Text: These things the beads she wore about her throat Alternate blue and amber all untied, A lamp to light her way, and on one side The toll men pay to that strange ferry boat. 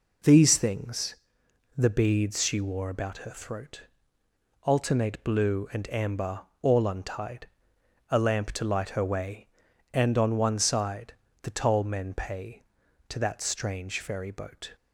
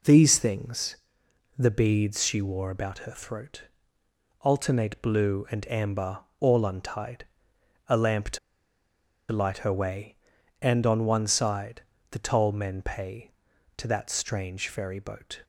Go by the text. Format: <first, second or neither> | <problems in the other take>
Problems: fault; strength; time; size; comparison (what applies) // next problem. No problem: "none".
first | pauses between "things" and "the"; noticeable; at 0.9 s; 0.62 s long; noticeable in the first // pauses between "throat" and "Alternate"; noticeable; at 3.6 s; 0.76 s long; noticeable in the first // pauses between "amber" and "all"; slight; at 6.1 s; 0.20 s long; slight in the first // pauses between "to" and "light"; noticeable; at 8.3 s; 0.93 s long // pauses between "side" and "The"; slight; at 11.8 s; 0.28 s long; slight in the first